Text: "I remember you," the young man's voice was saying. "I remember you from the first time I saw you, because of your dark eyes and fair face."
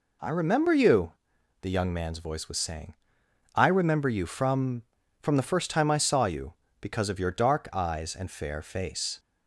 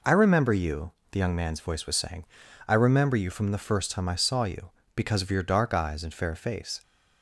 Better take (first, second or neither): second